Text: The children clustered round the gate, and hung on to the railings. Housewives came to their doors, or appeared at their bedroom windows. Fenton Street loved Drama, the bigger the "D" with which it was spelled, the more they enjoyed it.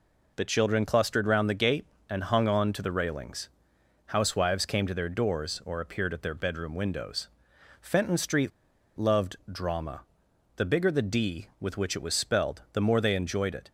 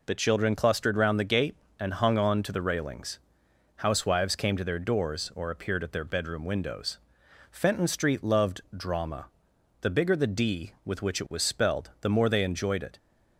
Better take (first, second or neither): second